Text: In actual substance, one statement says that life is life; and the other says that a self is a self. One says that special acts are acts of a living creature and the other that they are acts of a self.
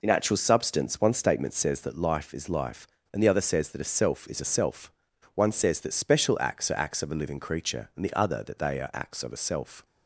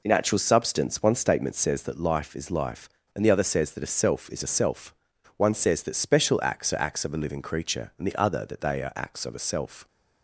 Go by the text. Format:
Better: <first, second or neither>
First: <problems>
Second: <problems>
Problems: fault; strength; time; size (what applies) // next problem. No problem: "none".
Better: neither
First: none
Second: none